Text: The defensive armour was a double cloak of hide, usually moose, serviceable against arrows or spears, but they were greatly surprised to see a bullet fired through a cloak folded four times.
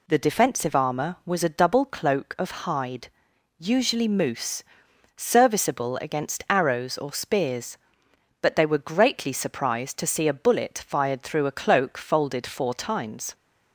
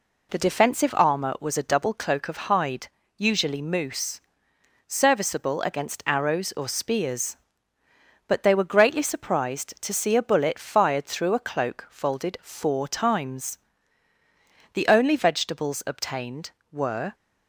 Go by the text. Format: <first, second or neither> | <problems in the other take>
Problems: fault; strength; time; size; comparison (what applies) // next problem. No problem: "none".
first | goes on to say "The only vegetables obtained were"; strong; from 14.7 s on; 2.4 s long